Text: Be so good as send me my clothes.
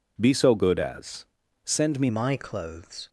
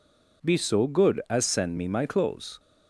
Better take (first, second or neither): second